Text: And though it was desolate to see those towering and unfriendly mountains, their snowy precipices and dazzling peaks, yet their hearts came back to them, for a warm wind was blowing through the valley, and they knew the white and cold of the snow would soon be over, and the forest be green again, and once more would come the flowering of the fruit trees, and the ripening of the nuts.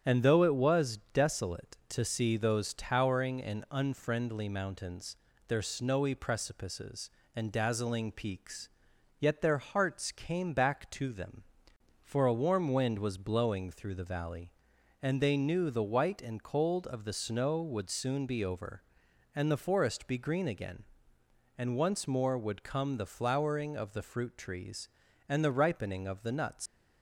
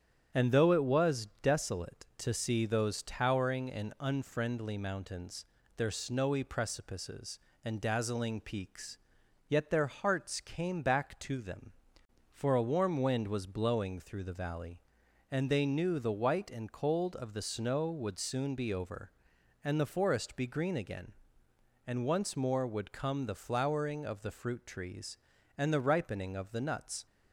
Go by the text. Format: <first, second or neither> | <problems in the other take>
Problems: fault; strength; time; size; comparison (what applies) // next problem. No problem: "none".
second | starts louder than the rest; strong; until 1.2 s; 9 dB; strong in the second // leaves "nuts" unfinished; at 26.6 s; 110 ms